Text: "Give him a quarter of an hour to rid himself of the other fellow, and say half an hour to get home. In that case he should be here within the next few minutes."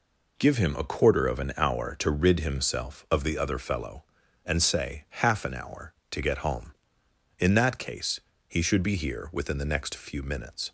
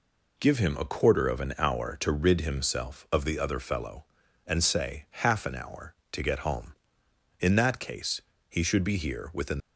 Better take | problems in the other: first | pauses between "case" and "he"; slight; at 8.2 s; 0.28 s long; slight in the first // stops before "the next few minutes"; at 9.5 s

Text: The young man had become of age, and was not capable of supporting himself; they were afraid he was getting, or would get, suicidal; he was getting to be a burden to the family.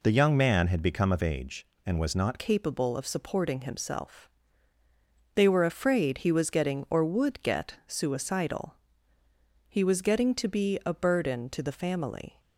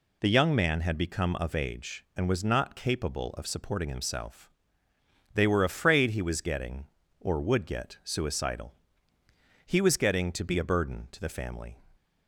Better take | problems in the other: second | changes voice at "capable"; from 2.3 s on; 10.0 s long

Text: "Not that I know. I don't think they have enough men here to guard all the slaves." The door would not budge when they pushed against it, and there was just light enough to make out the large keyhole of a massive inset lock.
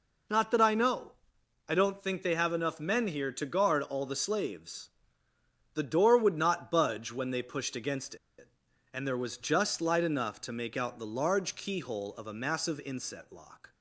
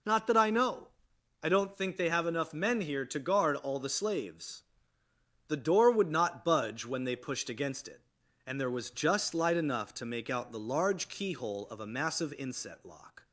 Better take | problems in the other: second | pauses between "against" and "it"; slight; at 8.1 s; 0.23 s long

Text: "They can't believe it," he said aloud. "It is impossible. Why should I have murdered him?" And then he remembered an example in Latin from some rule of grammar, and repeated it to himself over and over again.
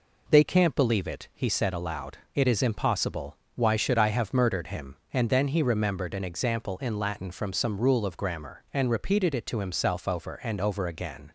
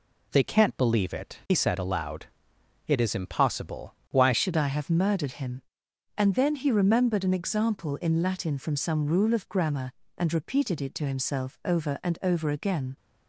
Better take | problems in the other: first | changes voice at "should"; from 4.3 s on; 8.6 s long

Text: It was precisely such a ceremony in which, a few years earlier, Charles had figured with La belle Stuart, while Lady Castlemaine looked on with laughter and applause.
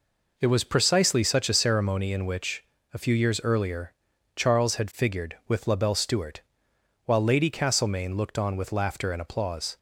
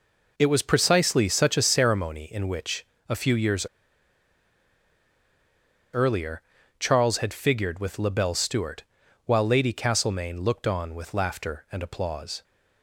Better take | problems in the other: first | pauses between "years" and "earlier"; strong; at 3.6 s; 2.2 s long

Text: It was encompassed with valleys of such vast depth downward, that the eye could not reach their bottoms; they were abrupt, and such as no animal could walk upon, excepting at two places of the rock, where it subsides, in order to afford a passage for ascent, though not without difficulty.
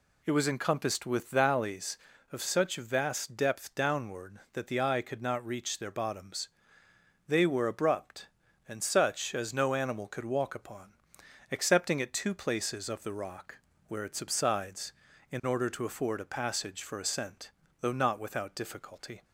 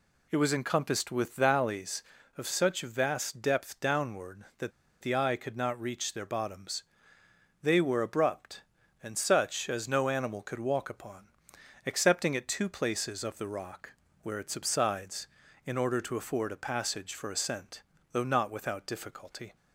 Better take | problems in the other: first | pauses between "that" and "the"; slight; at 4.7 s; 0.30 s long

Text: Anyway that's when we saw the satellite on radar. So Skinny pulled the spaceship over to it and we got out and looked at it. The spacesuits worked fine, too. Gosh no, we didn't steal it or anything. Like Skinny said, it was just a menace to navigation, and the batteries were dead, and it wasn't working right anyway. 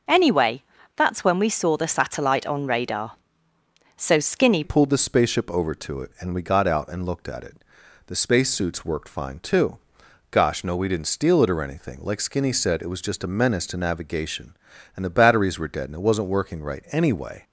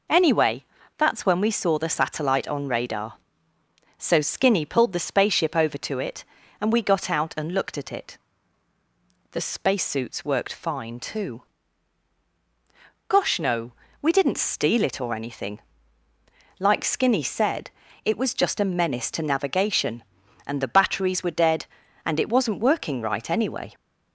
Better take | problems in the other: second | pauses between "Anyway" and "that's"; slight; at 0.6 s; 0.32 s long; slight in the second // changes voice at "pulled"; from 4.6 s on; 12.8 s long

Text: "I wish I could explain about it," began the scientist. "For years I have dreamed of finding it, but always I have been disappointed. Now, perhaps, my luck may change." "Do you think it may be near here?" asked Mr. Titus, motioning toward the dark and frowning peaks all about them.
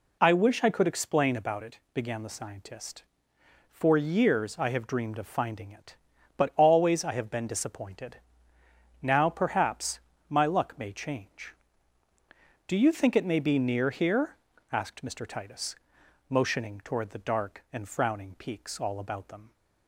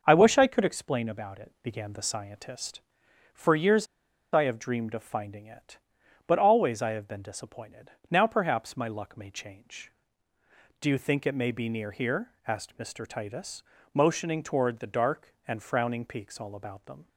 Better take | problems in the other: first | starts louder than the rest; noticeable; until 1.0 s; 6 dB // pauses between "years" and "I"; noticeable; at 3.8 s; 0.46 s long

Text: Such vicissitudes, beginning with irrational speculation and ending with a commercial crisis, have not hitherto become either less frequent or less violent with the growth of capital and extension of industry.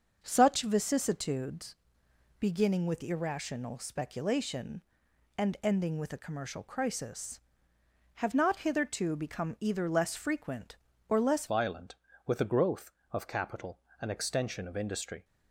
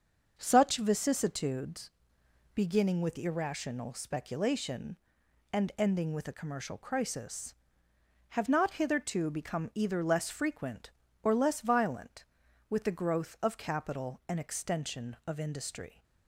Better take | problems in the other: second | starts louder than the rest; until 1.2 s; 6.5 dB; also in the second // changes voice at "violent"; from 11.4 s on; 3.8 s long

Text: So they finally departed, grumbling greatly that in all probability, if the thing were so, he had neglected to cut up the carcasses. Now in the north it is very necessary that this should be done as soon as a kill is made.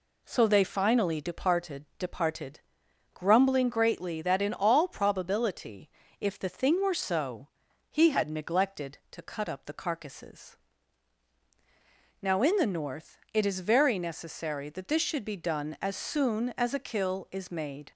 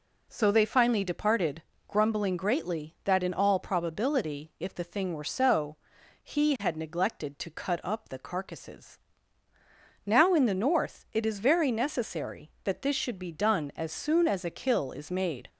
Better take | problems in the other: second | says "departed" twice; at 1.9 s // pauses between "north" and "it"; slight; at 13.1 s; 0.16 s long

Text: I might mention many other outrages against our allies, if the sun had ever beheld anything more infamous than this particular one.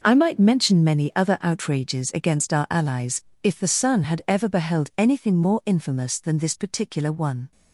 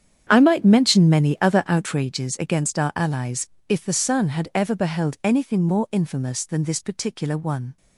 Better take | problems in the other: first | starts louder than the rest; strong; until 2.1 s; 8.5 dB

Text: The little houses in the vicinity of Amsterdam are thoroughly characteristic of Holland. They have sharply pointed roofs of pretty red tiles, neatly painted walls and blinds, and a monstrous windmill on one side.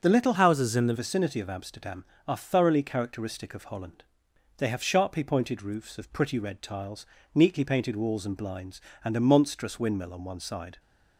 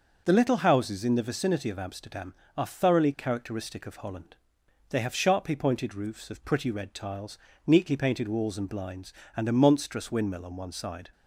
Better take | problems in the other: second | starts louder than the rest; until 1.0 s; 6 dB // changes voice from "houses" to "the"; from 0.3 to 0.9 s; 0.6 s long

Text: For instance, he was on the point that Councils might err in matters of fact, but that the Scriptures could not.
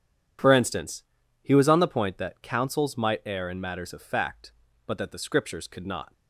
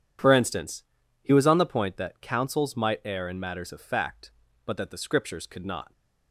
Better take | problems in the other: neither | none

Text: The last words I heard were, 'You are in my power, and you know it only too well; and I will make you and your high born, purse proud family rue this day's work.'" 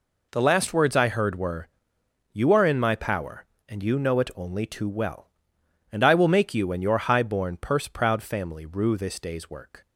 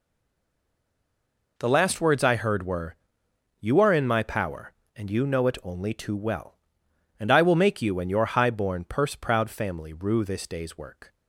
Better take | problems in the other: first | stays silent before the first word; noticeable; until 1.5 s; 1.5 s long

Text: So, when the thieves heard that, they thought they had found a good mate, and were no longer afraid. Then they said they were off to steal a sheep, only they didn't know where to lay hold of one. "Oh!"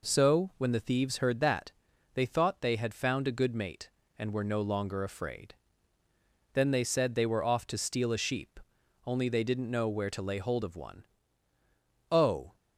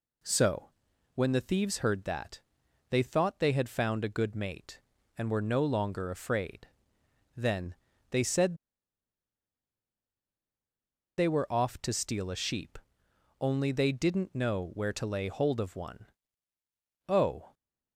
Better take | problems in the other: first | pauses between "Then" and "they"; slight; at 7.7 s; 0.36 s long // pauses between "said" and "they"; strong; at 8.5 s; 2.6 s long

